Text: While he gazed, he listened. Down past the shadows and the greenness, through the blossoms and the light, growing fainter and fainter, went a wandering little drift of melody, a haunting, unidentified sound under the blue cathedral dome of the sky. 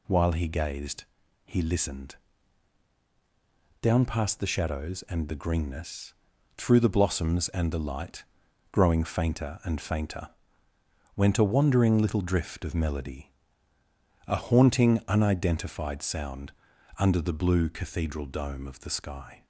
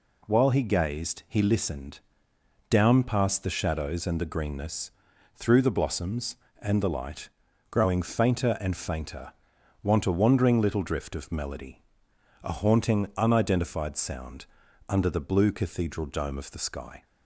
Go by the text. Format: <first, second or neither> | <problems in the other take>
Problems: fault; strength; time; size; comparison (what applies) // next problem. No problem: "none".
first | says "want" for "went"; at 9.8 s // pauses between "sound" and "under"; at 14.4 s; 0.42 s long; noticeable in the first